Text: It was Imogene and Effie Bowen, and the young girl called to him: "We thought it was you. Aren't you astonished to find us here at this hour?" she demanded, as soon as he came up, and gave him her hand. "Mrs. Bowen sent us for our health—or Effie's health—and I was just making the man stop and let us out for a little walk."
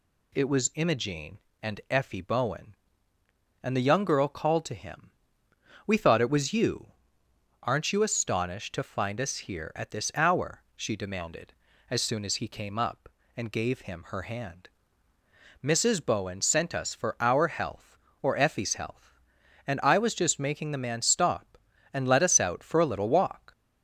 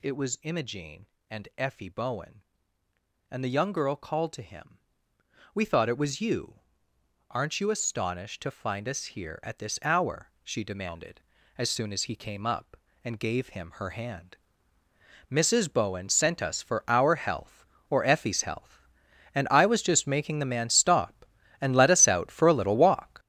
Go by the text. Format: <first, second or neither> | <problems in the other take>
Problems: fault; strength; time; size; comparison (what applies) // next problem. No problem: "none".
first | gets louder; strong; throughout; 9.5 dB